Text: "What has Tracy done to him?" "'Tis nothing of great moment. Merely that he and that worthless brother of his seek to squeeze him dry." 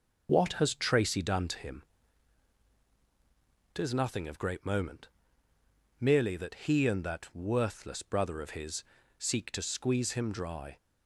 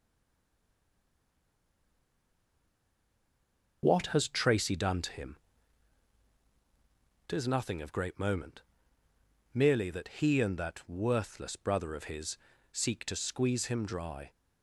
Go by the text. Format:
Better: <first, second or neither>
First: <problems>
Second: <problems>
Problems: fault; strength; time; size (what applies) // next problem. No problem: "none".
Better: first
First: pauses between "his" and "seek"; slight; at 8.8 s; 0.34 s long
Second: stays silent before the first word; strong; until 3.8 s; 3.8 s long // pauses between "his" and "seek"; slight; at 12.3 s; 0.34 s long